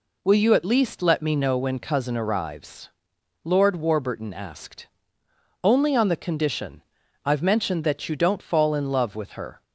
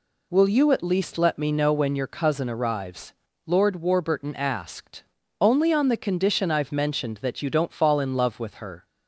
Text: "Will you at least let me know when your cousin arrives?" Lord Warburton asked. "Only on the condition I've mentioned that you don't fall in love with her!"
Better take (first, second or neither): second